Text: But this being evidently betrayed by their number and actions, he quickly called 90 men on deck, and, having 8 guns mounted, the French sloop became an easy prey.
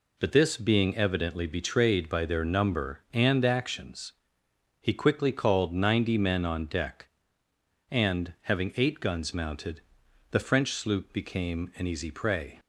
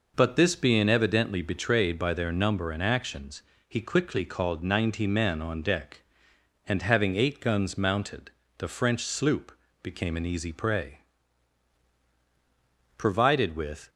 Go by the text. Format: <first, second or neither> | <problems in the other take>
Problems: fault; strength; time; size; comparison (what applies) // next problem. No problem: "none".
first | pauses between "sloop" and "became"; slight; at 9.5 s; 0.32 s long // goes on to say "Provided with"; noticeable; from 12.9 s on; 0.92 s long